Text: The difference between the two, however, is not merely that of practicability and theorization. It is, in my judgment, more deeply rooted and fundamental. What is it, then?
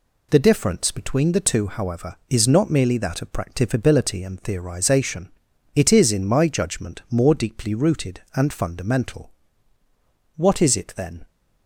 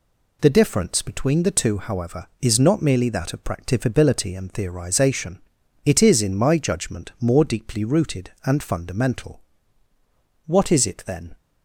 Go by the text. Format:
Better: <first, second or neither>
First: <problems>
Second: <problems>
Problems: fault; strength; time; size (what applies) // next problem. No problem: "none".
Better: neither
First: none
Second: none